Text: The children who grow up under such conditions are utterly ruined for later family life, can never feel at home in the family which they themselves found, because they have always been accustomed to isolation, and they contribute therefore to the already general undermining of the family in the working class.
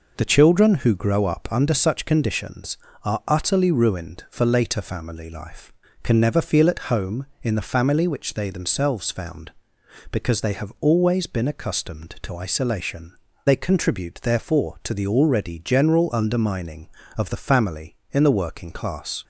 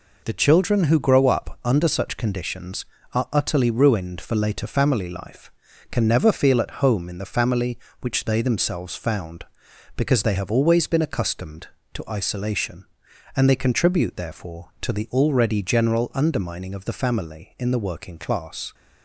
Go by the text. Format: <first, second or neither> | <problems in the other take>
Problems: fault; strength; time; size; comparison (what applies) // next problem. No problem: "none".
second | skips "and"; at 13.3 s